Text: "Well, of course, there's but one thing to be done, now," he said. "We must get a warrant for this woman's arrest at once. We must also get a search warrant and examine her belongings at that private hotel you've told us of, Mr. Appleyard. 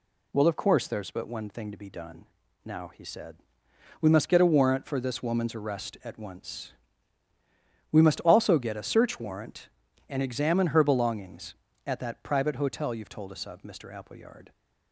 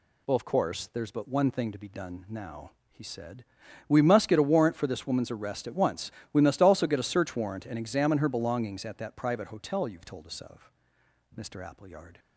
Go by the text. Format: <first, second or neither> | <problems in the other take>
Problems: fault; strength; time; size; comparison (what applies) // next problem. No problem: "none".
neither | none